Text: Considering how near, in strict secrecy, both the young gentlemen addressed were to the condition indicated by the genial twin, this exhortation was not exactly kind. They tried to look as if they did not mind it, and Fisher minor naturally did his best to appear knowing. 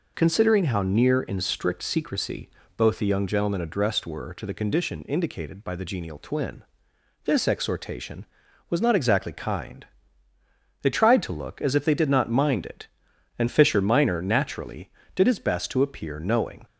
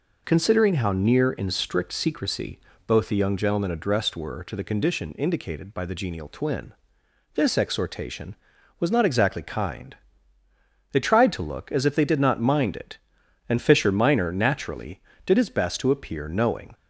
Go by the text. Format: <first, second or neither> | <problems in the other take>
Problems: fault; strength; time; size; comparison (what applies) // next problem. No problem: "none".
neither | none